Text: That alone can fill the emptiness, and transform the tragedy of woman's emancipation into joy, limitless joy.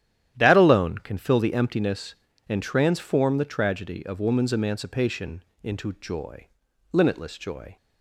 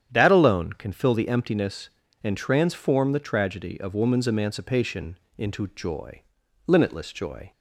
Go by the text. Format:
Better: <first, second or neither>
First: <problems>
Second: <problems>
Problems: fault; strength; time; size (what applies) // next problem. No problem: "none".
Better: second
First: gets quieter; strong; throughout; 12 dB // starts louder than the rest; strong; until 1.3 s; 11.5 dB // pauses between "emancipation" and "into"; slight; at 5.4 s; 0.20 s long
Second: starts louder than the rest; strong; until 1.1 s; 9 dB // pauses between "emancipation" and "into"; slight; at 5.1 s; 0.20 s long